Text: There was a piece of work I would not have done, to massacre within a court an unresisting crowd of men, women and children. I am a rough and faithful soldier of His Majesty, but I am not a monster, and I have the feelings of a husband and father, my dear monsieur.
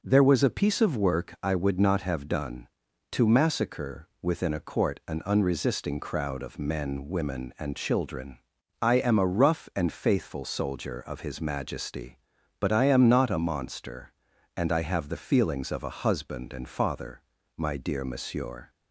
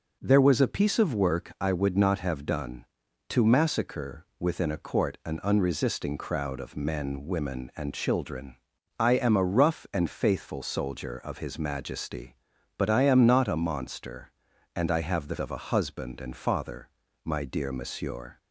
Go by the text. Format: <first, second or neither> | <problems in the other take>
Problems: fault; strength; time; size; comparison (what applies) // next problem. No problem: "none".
first | skips "feelings"; at 15.3 s